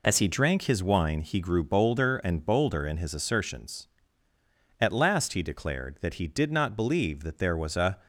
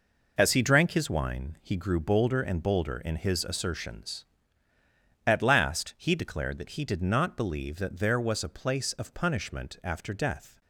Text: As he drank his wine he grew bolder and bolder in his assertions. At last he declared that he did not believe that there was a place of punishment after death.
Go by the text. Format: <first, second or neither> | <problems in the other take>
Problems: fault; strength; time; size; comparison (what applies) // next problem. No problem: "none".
second | stops before "place of punishment after death"; at 8.0 s